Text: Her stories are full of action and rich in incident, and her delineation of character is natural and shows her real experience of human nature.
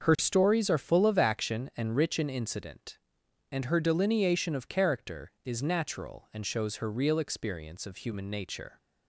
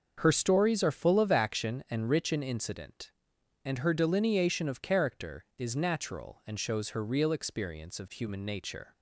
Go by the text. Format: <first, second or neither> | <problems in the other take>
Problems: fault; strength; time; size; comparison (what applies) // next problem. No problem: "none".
neither | starts louder than the rest; the same in both